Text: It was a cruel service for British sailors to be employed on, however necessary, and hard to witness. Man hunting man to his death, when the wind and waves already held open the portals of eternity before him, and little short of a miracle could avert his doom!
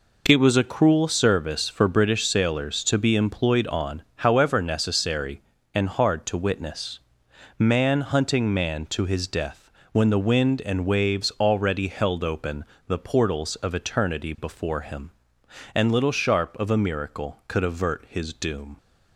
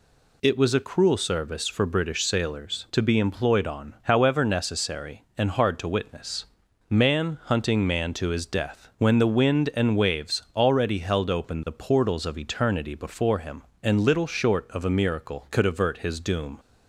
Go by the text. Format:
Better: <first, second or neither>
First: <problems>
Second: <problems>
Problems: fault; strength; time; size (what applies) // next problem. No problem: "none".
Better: second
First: pauses between "open" and "the"; slight; at 12.6 s; 0.24 s long // says "sharp" for "short"; at 16.1 s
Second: none